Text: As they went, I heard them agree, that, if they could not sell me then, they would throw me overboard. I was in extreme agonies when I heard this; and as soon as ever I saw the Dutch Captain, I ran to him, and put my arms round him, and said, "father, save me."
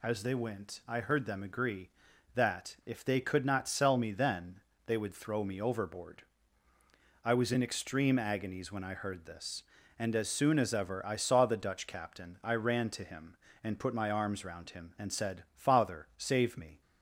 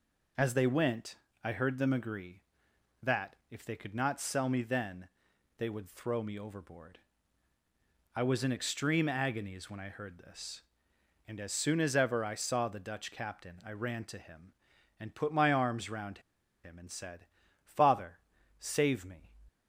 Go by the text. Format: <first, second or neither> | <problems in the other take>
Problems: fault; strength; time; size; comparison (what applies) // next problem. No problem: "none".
first | pauses between "round" and "him"; at 16.1 s; 0.44 s long